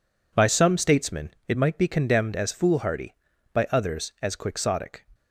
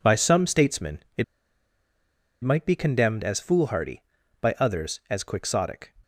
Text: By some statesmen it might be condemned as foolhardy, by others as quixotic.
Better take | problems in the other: first | pauses between "statesmen" and "it"; slight; at 1.0 s; 0.18 s long; slight in the first // pauses between "it" and "might"; at 1.2 s; 1.1 s long

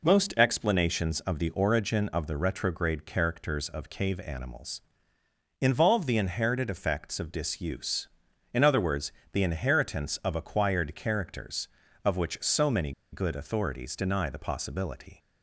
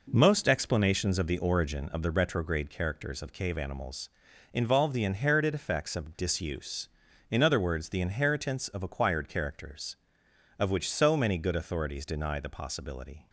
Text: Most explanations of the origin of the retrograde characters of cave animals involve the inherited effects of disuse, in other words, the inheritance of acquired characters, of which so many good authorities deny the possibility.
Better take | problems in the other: second | pauses between "animals" and "involve"; noticeable; at 4.8 s; 0.80 s long; noticeable in the second // pauses between "many" and "good"; slight; at 12.9 s; 0.20 s long

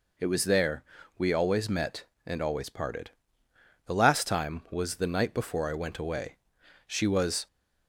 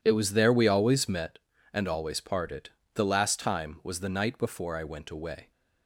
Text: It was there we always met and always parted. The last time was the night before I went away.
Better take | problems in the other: second | pauses between "there" and "we"; slight; at 0.8 s; 0.34 s long // goes on to say "She was"; from 6.8 s on; 0.60 s long

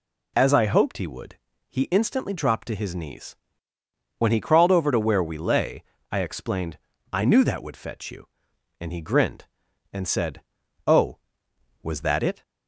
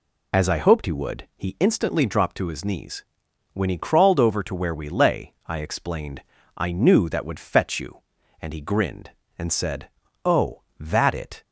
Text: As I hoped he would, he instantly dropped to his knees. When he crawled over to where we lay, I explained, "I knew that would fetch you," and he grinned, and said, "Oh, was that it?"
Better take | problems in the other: first | skips "was"; at 10.7 s

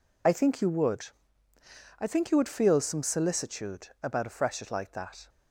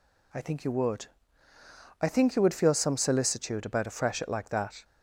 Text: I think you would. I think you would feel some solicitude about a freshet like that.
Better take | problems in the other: second | loses the start of "I"; at 0.2 s; 30 ms

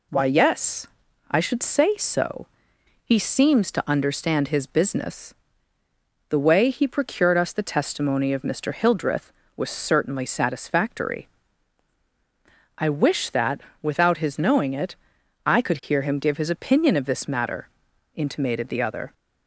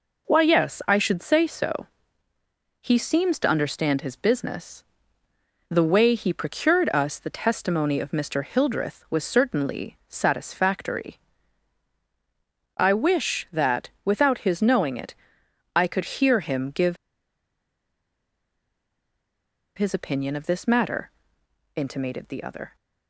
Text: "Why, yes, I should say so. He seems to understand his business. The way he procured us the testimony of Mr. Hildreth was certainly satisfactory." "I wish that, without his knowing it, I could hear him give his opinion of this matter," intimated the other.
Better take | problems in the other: first | pauses between "give" and "his"; strong; at 16.9 s; 2.7 s long

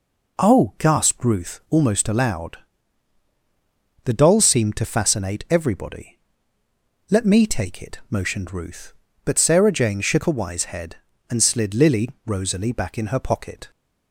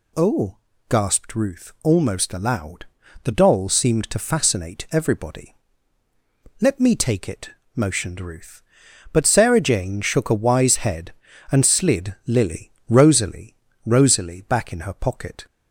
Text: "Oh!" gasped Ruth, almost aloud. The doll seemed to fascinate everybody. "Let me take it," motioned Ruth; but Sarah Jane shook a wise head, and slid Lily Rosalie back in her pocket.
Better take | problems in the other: first | pauses between "Lily" and "Rosalie"; slight; at 12.7 s; 0.18 s long; slight in the first // says "Rosalie" twice; at 13.8 s

